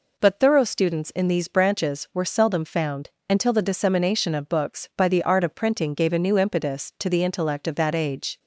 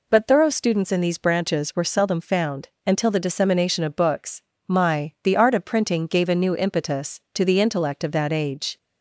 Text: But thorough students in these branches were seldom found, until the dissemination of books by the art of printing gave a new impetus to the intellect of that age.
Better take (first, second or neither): first